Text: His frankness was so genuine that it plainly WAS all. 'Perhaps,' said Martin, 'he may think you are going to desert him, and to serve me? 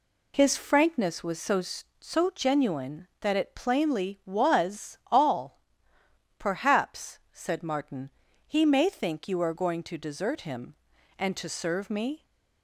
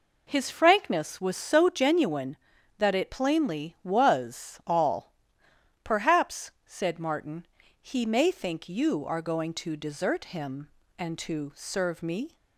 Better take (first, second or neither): second